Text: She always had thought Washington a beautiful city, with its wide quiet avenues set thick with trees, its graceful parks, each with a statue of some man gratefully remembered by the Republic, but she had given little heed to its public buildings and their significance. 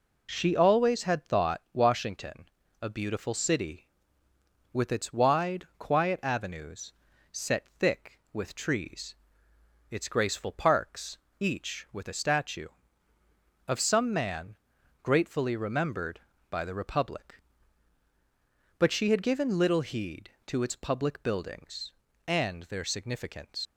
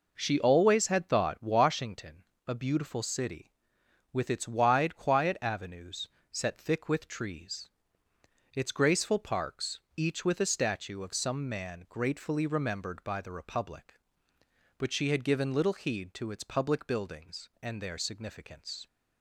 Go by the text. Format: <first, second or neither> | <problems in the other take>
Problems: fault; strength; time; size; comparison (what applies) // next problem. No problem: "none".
second | pauses between "Washington" and "a"; slight; at 2.4 s; 0.32 s long; slight in the second // pauses between "avenues" and "set"; at 6.9 s; 0.40 s long; slight in the second // pauses between "man" and "gratefully"; noticeable; at 14.5 s; 0.48 s long // leaves "significance" unfinished; at 23.6 s; 85 ms